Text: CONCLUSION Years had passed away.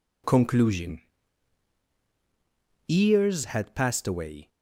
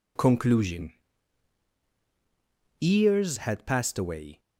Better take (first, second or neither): neither